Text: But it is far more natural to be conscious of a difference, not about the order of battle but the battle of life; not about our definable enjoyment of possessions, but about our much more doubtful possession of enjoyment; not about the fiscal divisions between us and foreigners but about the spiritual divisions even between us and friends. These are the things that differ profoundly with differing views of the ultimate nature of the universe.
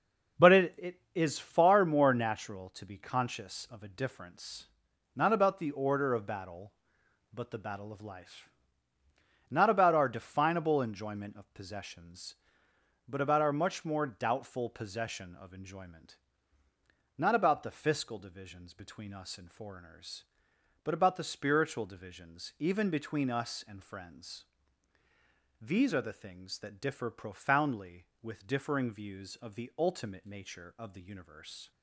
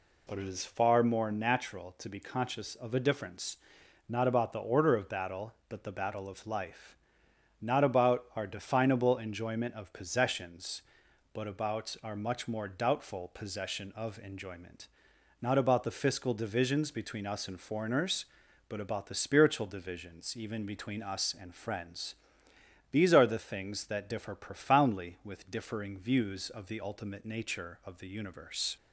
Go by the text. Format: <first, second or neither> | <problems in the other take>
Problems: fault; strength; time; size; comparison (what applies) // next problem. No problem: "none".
second | says "it" twice; at 0.7 s